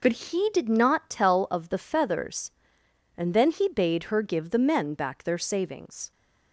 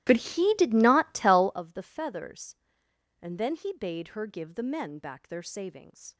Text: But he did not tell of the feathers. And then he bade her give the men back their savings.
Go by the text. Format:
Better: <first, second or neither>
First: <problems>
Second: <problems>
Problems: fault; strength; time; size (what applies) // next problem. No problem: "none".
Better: first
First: none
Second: starts louder than the rest; strong; until 1.6 s; 15 dB